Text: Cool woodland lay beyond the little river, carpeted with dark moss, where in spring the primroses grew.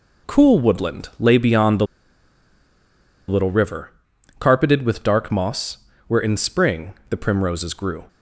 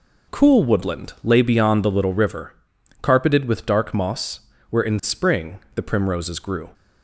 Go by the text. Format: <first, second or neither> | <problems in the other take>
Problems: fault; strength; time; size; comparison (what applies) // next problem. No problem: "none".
second | pauses between "the" and "little"; strong; at 1.8 s; 1.4 s long // pauses between "spring" and "the"; slight; at 6.9 s; 0.16 s long; slight in the second